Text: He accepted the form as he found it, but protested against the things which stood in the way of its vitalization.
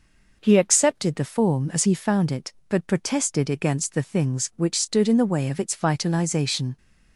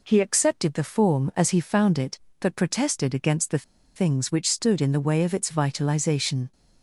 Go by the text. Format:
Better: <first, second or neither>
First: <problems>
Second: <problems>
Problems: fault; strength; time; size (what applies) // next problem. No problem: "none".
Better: first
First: none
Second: pauses between "the" and "things"; slight; at 3.6 s; 0.33 s long